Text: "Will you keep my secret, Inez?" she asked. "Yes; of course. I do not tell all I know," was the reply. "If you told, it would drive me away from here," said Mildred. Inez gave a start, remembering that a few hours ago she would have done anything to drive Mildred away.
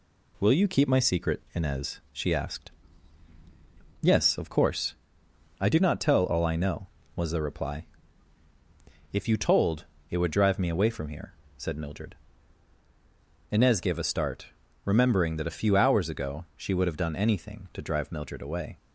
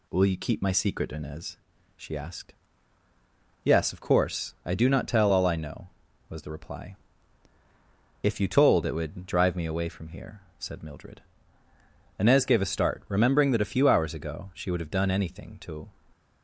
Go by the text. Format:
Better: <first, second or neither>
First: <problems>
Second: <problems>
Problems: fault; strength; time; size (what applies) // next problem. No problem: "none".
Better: first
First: none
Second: stops before "drive Mildred away"; at 16.1 s